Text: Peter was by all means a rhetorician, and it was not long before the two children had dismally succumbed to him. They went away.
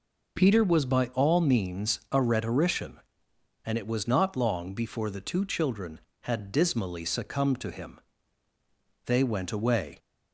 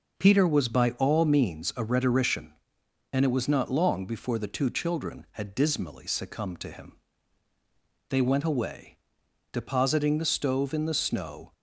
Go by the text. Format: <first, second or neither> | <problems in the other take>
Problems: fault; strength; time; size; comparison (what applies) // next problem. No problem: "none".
first | goes on to say "Depositing the stove in the snow"; strong; from 9.5 s on; 2.0 s long